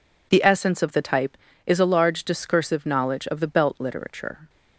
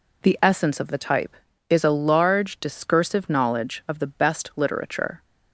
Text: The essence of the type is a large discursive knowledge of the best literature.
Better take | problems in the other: second | says "belt" for "best"; at 3.4 s

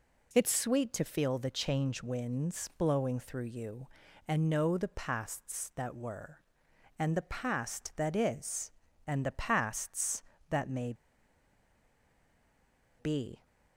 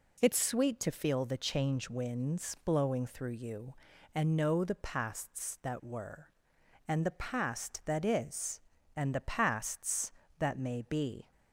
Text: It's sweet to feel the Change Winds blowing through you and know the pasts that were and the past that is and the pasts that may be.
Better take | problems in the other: second | pauses between "may" and "be"; strong; at 10.9 s; 2.0 s long

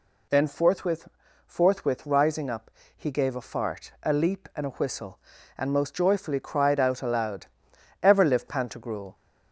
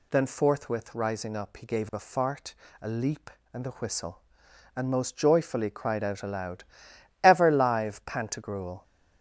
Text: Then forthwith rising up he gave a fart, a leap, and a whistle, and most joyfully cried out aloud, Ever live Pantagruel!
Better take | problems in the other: second | says "forthwith" twice; at 1.4 s // pauses between "up" and "he"; slight; at 2.7 s; 0.26 s long

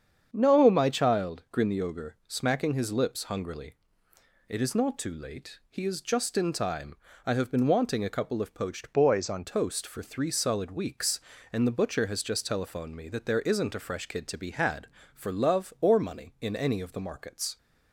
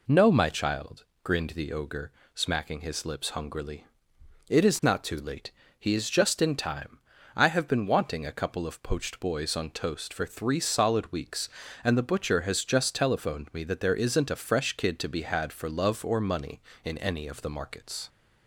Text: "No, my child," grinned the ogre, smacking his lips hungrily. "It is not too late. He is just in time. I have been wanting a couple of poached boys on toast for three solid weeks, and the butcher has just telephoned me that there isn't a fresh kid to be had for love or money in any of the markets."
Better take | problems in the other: second | starts louder than the rest; strong; until 1.3 s; 7.5 dB // changes voice from "boys" to "on"; from 8.9 to 9.4 s; 0.5 s long

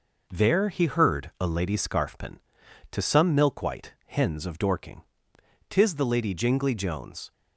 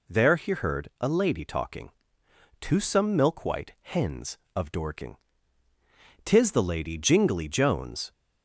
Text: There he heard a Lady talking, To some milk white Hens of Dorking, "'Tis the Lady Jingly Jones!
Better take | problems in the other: second | says "scarfpin" for "talking"; at 1.7 s

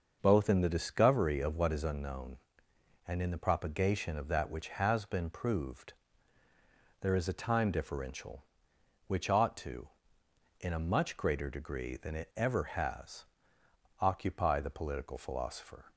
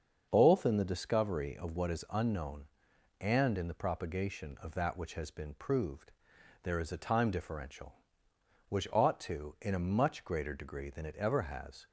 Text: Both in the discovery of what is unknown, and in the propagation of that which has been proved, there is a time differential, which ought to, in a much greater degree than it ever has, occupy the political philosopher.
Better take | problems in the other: first | starts louder than the rest; until 1.3 s; 6.5 dB; noticeable in the first // stops before "occupy the political philosopher"; at 11.8 s

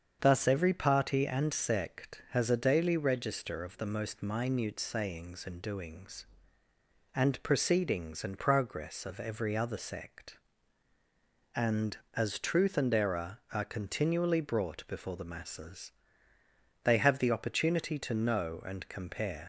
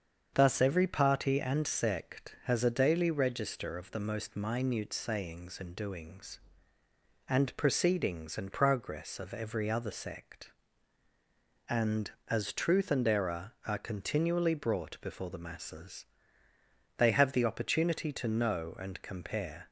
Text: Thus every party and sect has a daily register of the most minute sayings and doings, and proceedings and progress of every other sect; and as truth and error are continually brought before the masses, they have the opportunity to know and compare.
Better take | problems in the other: second | starts louder than the rest; strong; until 1.2 s; 7 dB; strong in the second // leaves "compare" unfinished; at 19.4 s; 75 ms

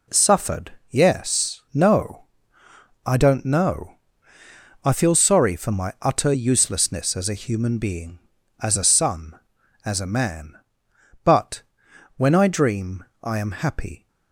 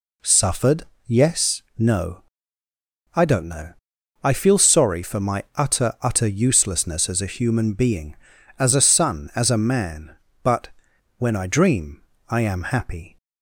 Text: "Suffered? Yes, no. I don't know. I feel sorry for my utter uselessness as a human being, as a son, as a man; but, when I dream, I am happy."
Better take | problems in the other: first | says "utter" twice; at 6.0 s

